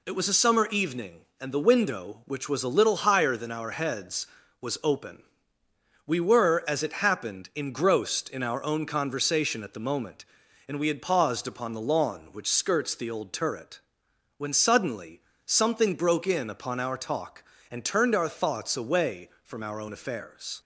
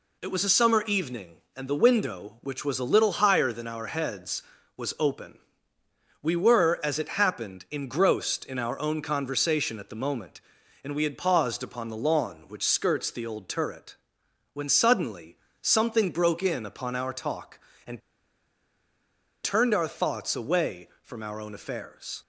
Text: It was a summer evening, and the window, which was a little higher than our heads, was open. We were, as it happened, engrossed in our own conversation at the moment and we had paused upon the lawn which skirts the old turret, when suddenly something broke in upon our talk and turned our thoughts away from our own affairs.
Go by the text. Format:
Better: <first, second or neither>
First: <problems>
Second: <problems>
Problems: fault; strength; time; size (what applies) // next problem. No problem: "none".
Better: first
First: pauses between "suddenly" and "something"; slight; at 15.1 s; 0.26 s long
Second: pauses between "suddenly" and "something"; slight; at 15.3 s; 0.26 s long // pauses between "and" and "turned"; strong; at 17.9 s; 1.4 s long